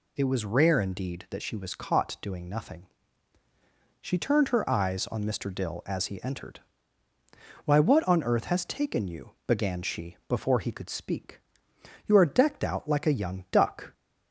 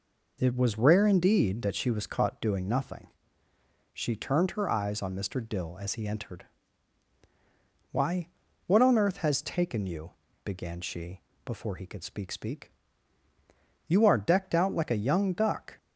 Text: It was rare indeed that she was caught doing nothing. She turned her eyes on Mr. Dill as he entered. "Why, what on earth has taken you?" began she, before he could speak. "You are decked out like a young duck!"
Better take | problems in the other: first | says "speak" twice; at 12.3 s

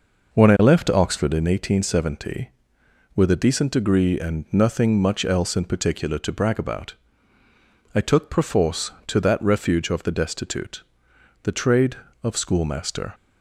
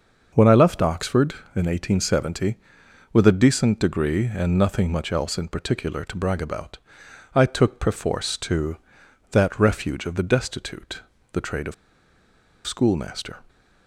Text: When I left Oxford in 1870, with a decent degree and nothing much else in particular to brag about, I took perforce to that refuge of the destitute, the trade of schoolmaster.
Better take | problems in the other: first | starts louder than the rest; until 1.3 s; 6 dB // pauses between "of" and "schoolmaster"; noticeable; at 11.7 s; 0.93 s long

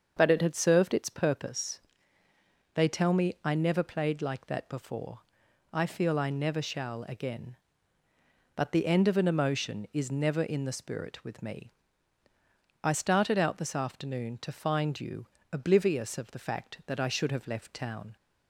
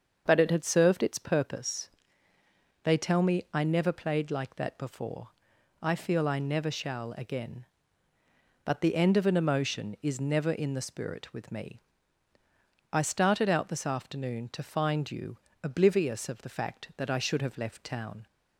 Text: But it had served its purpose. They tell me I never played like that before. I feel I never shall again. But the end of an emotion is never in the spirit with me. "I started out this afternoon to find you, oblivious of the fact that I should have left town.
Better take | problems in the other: neither | starts louder than the rest; the same in both

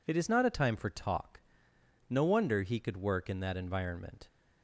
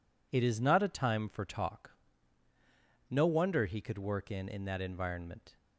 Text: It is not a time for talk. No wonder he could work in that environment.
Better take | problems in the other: first | says "in" twice; at 4.4 s

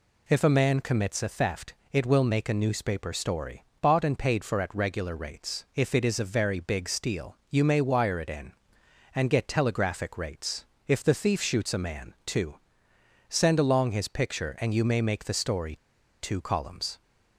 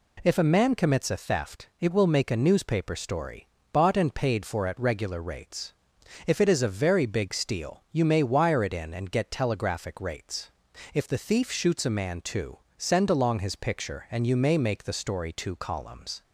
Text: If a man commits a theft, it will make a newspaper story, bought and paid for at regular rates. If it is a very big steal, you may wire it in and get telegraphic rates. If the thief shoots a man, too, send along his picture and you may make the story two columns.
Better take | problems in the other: second | pauses between "story" and "two"; noticeable; at 15.7 s; 0.46 s long

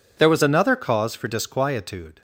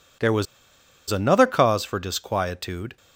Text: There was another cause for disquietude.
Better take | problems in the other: first | pauses between "was" and "another"; noticeable; at 0.4 s; 0.65 s long

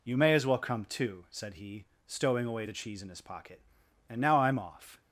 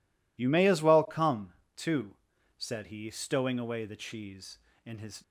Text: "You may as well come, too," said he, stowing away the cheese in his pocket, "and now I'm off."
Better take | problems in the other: first | stops before "pocket and now I'm off"; at 5.2 s

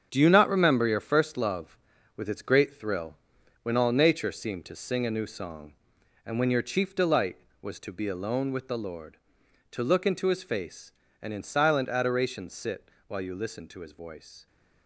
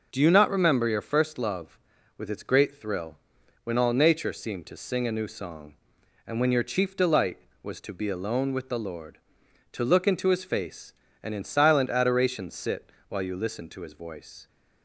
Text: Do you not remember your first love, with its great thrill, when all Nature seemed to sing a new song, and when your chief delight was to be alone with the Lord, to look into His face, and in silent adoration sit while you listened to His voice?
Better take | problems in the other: second | gets quieter; strong; throughout; 9.5 dB // pauses between "sit" and "while"; slight; at 12.8 s; 0.20 s long; slight in the second

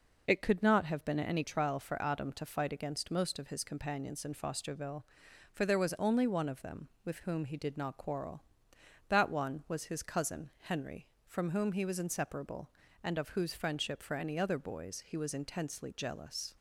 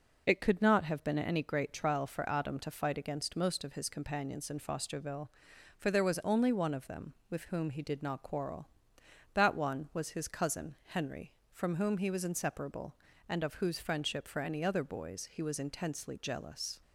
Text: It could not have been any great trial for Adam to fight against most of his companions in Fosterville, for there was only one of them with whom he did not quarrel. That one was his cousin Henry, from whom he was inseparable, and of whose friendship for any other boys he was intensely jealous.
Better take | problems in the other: second | skips "great"; at 1.4 s

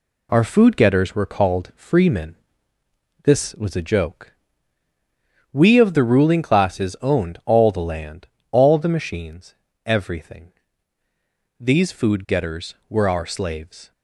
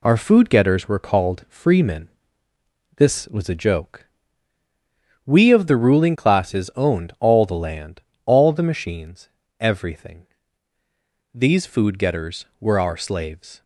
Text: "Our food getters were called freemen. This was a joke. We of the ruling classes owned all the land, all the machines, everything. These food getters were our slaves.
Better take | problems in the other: neither | none

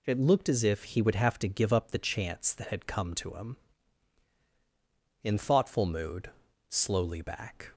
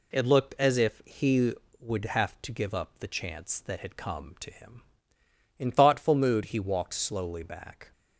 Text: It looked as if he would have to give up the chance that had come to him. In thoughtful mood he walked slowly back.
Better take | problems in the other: second | skips "he walked"; at 6.4 s

